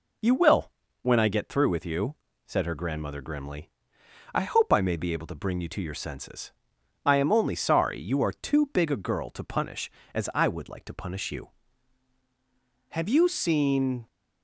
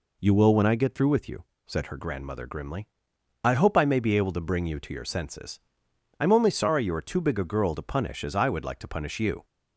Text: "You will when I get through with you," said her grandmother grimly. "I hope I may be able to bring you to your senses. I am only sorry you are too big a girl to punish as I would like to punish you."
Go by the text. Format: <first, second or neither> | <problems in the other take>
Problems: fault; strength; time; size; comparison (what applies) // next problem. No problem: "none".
second | pauses between "will" and "when"; slight; at 0.7 s; 0.32 s long // goes on to say "Have you seen"; noticeable; from 12.8 s on; 1.1 s long